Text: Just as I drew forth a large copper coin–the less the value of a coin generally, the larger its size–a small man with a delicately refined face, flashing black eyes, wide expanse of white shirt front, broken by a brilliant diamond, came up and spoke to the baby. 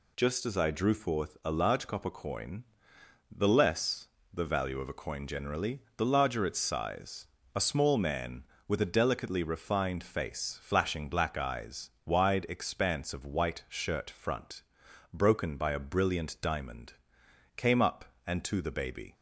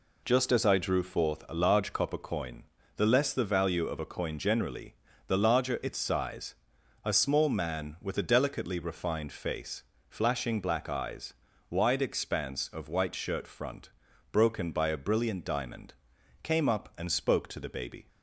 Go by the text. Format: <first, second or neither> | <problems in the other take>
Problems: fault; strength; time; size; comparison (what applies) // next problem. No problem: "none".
second | pauses between "less" and "the"; slight; at 4.0 s; 0.24 s long // skips "spoke"; at 18.4 s